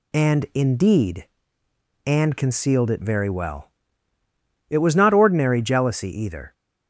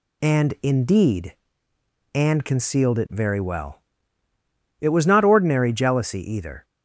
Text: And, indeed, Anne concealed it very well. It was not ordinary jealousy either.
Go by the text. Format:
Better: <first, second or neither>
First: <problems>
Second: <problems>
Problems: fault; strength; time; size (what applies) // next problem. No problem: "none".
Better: neither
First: none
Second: none